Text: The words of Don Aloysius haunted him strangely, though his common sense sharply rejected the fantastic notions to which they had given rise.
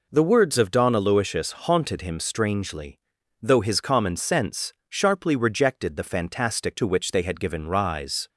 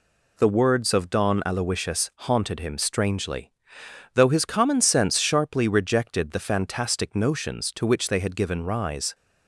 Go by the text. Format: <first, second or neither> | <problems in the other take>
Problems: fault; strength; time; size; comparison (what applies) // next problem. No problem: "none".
second | pauses between "sense" and "sharply"; slight; at 4.7 s; 0.16 s long // skips "notions"; at 6.7 s